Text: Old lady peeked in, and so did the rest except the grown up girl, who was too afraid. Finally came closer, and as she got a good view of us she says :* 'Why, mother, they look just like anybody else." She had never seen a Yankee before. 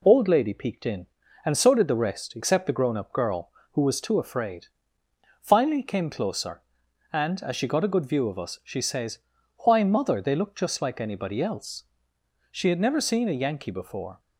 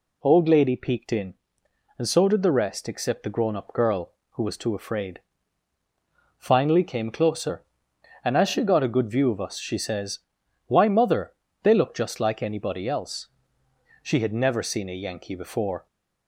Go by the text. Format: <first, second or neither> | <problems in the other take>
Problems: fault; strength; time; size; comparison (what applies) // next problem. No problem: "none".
neither | none